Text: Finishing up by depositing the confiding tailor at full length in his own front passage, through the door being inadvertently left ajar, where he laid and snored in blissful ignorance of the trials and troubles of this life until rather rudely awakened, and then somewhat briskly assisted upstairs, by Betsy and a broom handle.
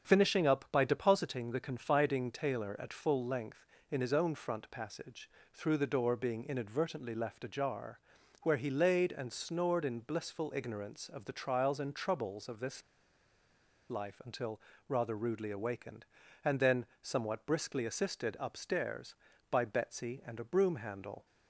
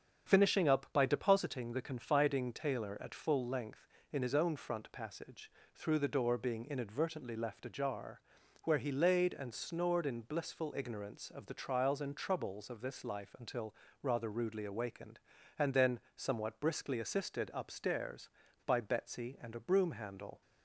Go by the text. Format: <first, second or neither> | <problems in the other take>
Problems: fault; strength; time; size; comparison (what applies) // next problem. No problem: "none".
second | starts louder than the rest; strong; until 1.1 s; 7.5 dB; strong in the second // pauses between "this" and "life"; at 12.8 s; 1.0 s long // pauses between "until" and "rather"; slight; at 14.5 s; 0.30 s long; slight in the second // pauses between "then" and "somewhat"; slight; at 16.8 s; 0.20 s long; slight in the second